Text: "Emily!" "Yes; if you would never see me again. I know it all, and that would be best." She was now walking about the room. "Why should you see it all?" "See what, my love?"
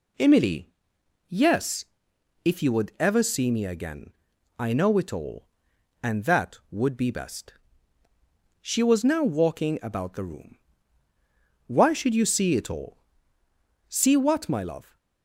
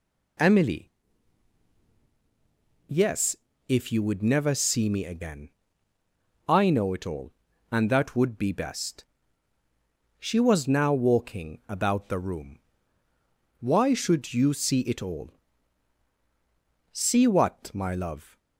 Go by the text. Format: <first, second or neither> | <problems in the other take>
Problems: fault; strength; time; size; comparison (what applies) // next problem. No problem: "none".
second | says "ever" for "never"; at 3.0 s